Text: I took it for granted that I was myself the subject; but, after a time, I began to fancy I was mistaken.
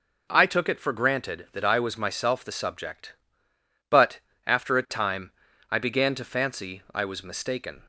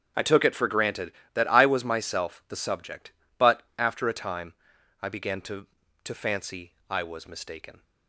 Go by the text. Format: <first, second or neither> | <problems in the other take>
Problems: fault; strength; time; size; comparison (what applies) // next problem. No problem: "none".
first | starts louder than the rest; strong; until 1.4 s; 8 dB // says "to" twice; at 6.0 s // pauses between "fancy" and "I"; slight; at 6.7 s; 0.16 s long